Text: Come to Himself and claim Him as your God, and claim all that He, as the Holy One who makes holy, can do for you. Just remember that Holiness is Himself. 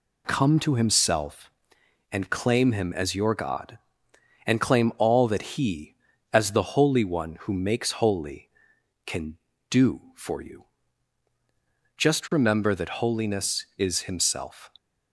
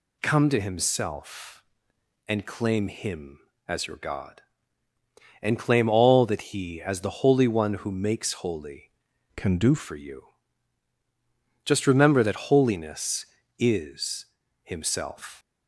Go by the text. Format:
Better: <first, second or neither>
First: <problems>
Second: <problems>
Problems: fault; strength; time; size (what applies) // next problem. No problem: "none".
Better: first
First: none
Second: changes voice from "can" to "do"; from 9.3 to 9.7 s; 0.4 s long // pauses between "is" and "Himself"; slight; at 14.2 s; 0.36 s long